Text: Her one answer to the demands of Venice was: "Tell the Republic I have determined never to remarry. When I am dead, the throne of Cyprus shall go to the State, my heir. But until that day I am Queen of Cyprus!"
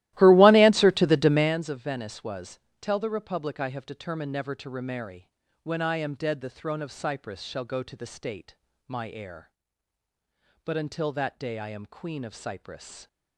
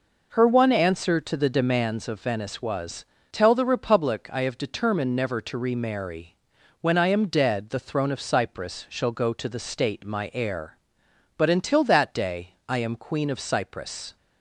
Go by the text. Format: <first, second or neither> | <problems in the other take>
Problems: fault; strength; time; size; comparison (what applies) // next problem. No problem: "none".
second | starts louder than the rest; strong; until 1.6 s; 16 dB